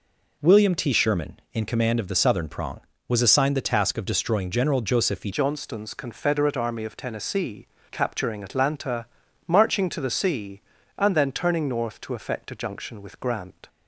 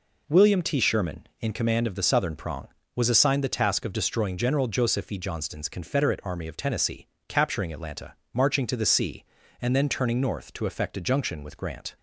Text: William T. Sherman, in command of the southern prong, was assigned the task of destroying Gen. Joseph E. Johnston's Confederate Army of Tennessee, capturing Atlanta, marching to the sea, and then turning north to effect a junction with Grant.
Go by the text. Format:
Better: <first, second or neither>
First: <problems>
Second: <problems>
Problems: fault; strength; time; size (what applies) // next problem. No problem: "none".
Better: second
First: changes voice at "Johnston's"; from 5.3 s on; 8.3 s long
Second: none